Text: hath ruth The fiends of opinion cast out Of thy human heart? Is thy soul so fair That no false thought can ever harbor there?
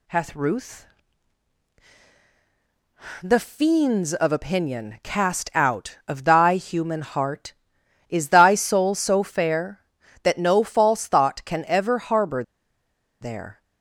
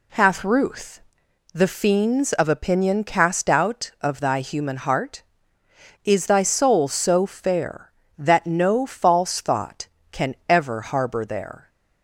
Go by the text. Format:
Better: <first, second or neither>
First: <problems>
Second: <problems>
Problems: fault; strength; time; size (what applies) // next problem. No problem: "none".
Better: second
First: pauses between "ruth" and "The"; strong; at 0.8 s; 2.3 s long // pauses between "harbor" and "there"; noticeable; at 12.4 s; 0.77 s long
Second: pauses between "ruth" and "The"; noticeable; at 1.0 s; 0.52 s long